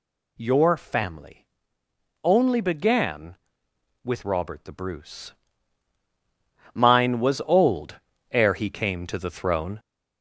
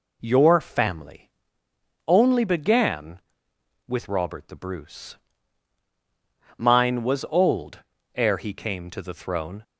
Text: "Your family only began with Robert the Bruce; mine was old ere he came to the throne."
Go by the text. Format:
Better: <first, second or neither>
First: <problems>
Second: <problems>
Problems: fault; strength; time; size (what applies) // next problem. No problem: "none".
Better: second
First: gets louder; noticeable; throughout; 4.5 dB // pauses between "family" and "only"; noticeable; at 1.4 s; 0.76 s long // pauses between "old" and "ere"; slight; at 7.9 s; 0.34 s long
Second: pauses between "family" and "only"; noticeable; at 1.3 s; 0.76 s long // pauses between "old" and "ere"; slight; at 7.7 s; 0.34 s long